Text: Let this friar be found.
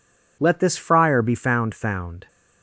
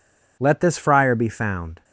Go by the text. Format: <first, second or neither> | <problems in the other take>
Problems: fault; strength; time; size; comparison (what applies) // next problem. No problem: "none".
second | says "found" twice; at 1.7 s